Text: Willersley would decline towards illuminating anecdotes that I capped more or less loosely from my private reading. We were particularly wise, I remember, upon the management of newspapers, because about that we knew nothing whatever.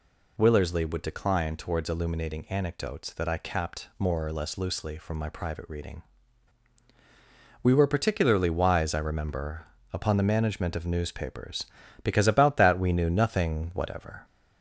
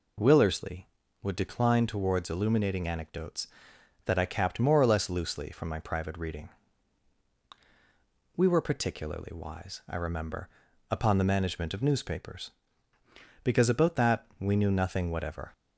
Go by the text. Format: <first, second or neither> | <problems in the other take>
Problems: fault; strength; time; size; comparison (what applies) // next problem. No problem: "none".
second | gets louder; slight; throughout; 2.5 dB